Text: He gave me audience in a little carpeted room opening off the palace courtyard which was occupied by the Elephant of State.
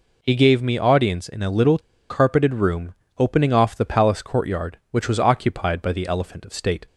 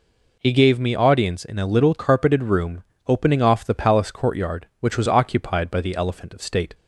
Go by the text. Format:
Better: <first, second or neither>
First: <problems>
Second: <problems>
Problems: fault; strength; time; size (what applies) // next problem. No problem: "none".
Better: second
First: pauses between "little" and "carpeted"; slight; at 1.7 s; 0.30 s long // pauses between "room" and "opening"; slight; at 2.9 s; 0.24 s long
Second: pauses between "room" and "opening"; slight; at 2.8 s; 0.24 s long